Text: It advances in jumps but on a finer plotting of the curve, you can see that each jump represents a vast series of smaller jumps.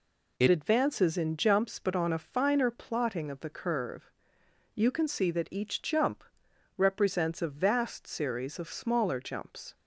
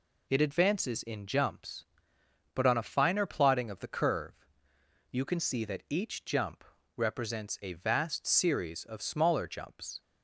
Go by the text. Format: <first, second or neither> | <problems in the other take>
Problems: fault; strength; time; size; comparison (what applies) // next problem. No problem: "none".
second | changes voice at "advances"; from 0.4 s on; 9.3 s long // pauses between "jump" and "represents"; noticeable; at 6.2 s; 0.54 s long; slight in the second